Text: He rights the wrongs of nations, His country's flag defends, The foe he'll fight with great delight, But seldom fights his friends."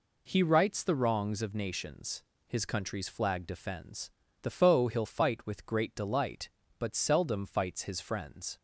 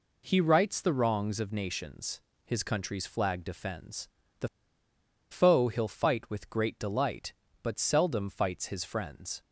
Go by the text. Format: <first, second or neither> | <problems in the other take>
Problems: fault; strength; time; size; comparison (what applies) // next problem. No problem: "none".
first | pauses between "The" and "foe"; noticeable; at 4.4 s; 0.82 s long